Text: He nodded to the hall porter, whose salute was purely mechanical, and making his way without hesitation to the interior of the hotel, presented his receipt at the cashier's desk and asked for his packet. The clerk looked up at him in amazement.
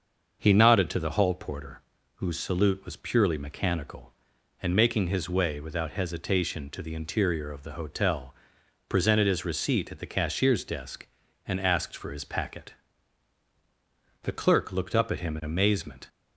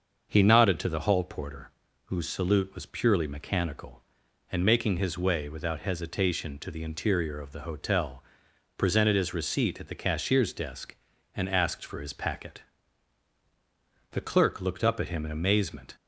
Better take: neither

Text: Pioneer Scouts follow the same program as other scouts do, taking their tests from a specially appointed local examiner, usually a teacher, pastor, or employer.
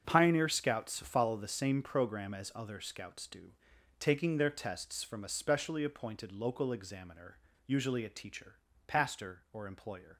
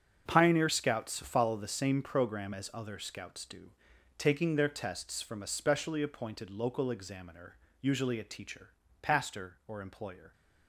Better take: neither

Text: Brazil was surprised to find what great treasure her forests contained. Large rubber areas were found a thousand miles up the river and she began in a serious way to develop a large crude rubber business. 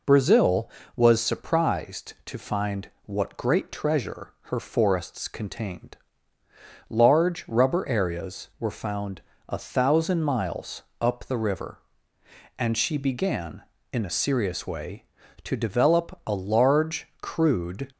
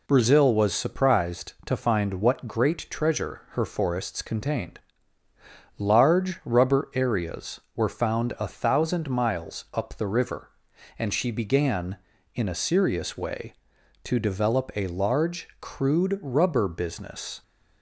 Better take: second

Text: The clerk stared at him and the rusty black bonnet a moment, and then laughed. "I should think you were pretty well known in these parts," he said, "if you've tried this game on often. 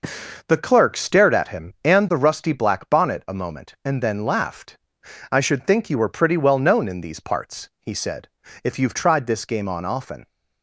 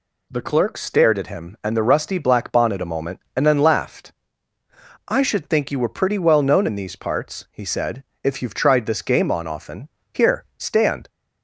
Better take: first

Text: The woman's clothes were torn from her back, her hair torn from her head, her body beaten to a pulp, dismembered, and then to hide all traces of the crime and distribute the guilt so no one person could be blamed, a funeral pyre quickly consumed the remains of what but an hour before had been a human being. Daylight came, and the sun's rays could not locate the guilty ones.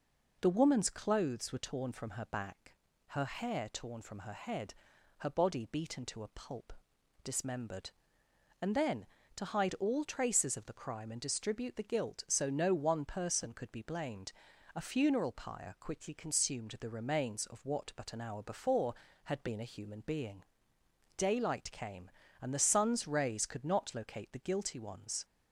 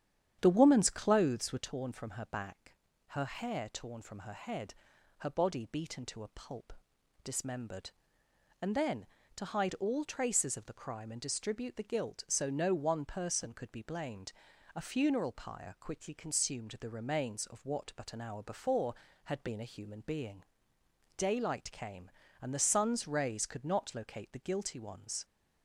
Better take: first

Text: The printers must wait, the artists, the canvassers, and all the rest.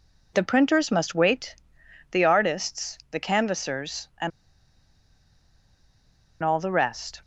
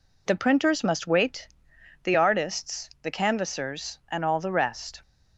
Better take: second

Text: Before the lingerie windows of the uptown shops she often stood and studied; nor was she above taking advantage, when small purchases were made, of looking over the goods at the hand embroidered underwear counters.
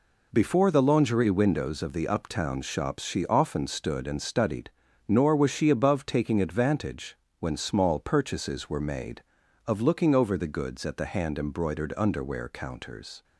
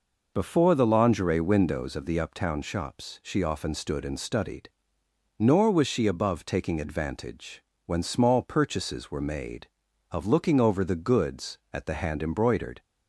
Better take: first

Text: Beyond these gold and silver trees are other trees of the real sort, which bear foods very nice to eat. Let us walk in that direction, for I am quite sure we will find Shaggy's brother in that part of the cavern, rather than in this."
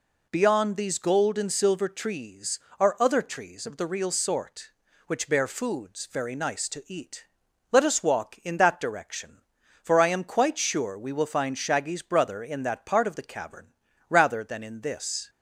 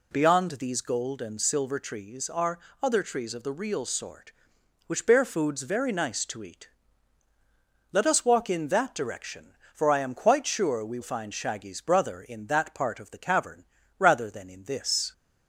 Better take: first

